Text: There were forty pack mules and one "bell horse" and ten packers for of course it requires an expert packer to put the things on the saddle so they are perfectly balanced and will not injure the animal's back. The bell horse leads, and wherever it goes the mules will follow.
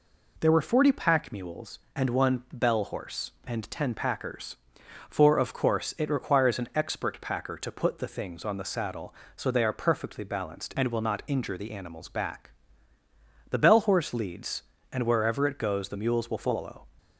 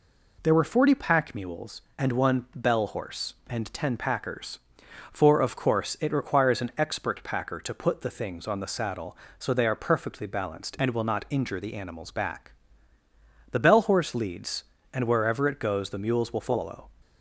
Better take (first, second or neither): neither